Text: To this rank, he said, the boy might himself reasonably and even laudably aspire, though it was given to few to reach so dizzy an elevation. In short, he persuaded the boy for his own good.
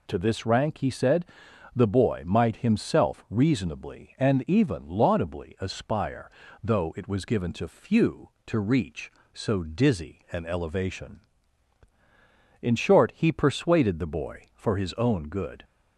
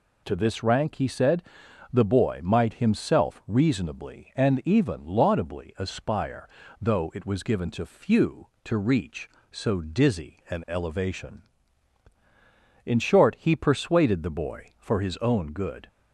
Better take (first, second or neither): neither